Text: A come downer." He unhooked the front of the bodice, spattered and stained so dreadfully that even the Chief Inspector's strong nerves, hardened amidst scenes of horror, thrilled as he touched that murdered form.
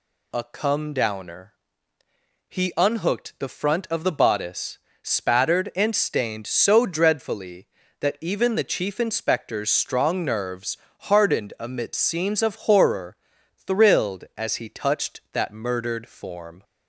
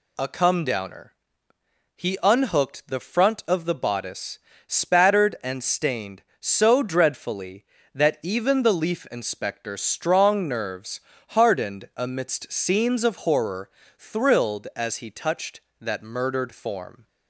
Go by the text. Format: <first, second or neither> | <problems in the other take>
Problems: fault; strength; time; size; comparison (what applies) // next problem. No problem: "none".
first | says "Leaf" for "Chief"; at 8.7 s